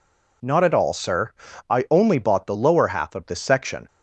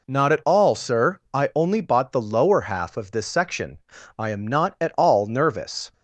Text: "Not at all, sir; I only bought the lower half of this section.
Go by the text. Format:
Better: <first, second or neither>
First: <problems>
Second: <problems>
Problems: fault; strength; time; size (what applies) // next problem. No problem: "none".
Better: first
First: none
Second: goes on to say "I am not at all nervous"; strong; from 4.1 s on; 1.7 s long